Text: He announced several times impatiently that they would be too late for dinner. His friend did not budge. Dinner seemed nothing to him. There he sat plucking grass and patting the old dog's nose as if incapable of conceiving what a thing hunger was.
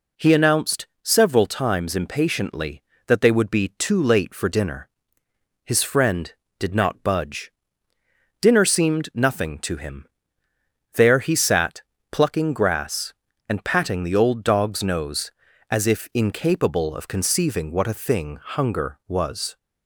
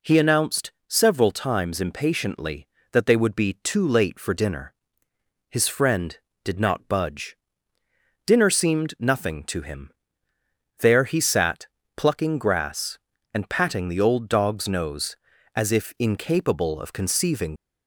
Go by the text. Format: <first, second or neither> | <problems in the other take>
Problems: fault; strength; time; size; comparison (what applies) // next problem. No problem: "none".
first | pauses between "announced" and "several"; slight; at 0.7 s; 0.16 s long; slight in the first // pauses between "sat" and "plucking"; slight; at 11.6 s; 0.30 s long; slight in the first // stops before "what a thing hunger was"; at 17.5 s